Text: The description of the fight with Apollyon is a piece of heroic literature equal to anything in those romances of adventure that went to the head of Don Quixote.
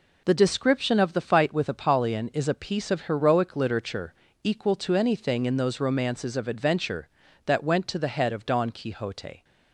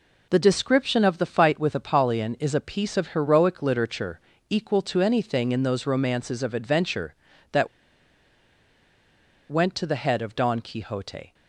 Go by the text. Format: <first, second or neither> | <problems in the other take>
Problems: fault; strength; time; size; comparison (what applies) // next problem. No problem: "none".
first | pauses between "literature" and "equal"; slight; at 4.2 s; 0.30 s long; slight in the first // pauses between "that" and "went"; strong; at 7.6 s; 1.8 s long